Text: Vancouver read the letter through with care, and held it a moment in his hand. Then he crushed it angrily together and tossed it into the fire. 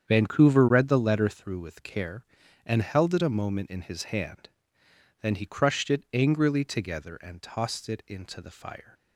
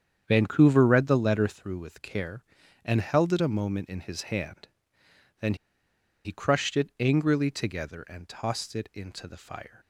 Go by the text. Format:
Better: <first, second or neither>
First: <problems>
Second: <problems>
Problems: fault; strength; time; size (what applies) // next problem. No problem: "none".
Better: first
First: starts louder than the rest; strong; until 1.1 s; 8 dB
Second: starts louder than the rest; strong; until 1.2 s; 8 dB // pauses between "Then" and "he"; noticeable; at 5.5 s; 0.70 s long